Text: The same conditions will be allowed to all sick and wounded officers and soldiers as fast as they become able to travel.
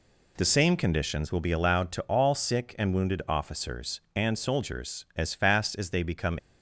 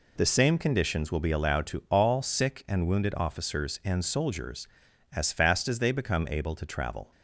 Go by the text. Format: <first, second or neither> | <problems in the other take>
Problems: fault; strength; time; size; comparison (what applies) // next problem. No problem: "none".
second | stops before "able to travel"; at 6.3 s